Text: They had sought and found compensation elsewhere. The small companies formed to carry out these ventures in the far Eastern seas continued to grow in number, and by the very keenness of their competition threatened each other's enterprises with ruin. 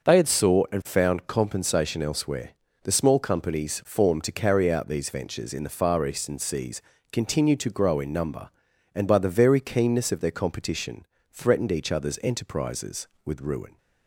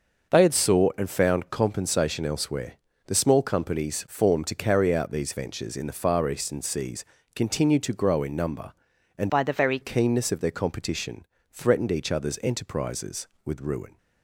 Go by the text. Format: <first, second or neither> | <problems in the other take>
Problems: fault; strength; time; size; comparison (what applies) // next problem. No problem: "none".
first | starts louder than the rest; noticeable; until 1.3 s; 6 dB // pauses between "seas" and "continued"; slight; at 7.0 s; 0.28 s long; slight in the first // changes voice from "by" to "very"; from 9.2 to 9.7 s; 0.5 s long // pauses between "competition" and "threatened"; slight; at 11.2 s; 0.24 s long; slight in the first